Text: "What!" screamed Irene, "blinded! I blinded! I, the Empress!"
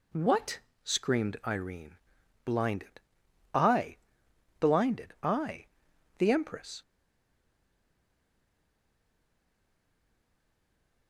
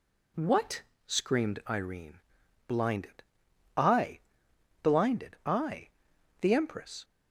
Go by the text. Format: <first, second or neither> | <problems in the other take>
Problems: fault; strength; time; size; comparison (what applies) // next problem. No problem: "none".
second | pauses between "I" and "blinded"; noticeable; at 3.9 s; 0.64 s long; noticeable in the second // stays silent after the last word; strong; from 6.8 s on; 4.2 s long